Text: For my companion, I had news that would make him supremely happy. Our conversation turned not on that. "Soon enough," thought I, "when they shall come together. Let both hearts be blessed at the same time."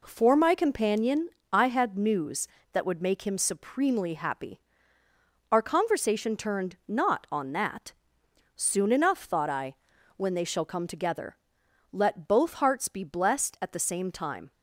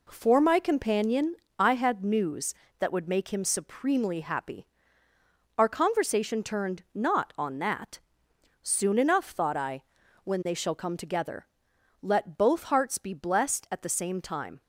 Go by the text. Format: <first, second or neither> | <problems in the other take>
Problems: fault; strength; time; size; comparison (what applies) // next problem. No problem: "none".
neither | none